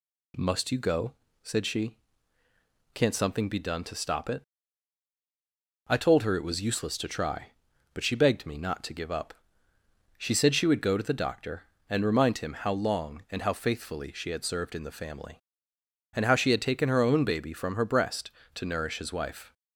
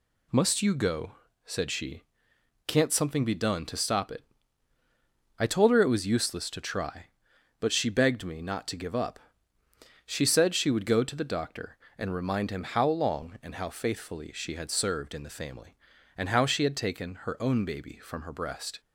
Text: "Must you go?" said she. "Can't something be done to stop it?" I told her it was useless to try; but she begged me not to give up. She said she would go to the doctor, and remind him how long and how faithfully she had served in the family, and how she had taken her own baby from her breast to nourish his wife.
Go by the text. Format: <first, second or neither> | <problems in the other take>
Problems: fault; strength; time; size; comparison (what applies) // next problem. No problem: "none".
first | stops before "to nourish his wife"; at 18.8 s